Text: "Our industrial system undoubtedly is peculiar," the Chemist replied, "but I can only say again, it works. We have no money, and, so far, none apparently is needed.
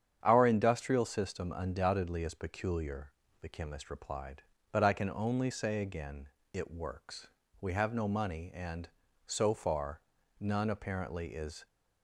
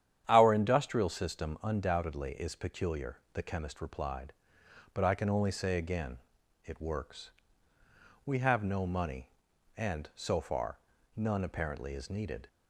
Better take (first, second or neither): second